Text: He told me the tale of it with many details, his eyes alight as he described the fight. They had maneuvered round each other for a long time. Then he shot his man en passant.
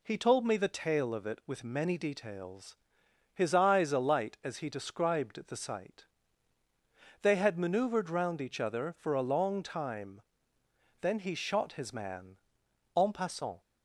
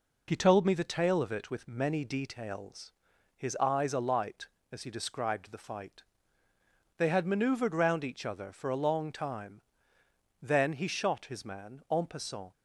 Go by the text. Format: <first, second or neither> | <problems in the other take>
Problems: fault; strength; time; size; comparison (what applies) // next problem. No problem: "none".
second | says "sight" for "fight"; at 5.5 s // pauses between "man" and "en"; noticeable; at 12.3 s; 0.60 s long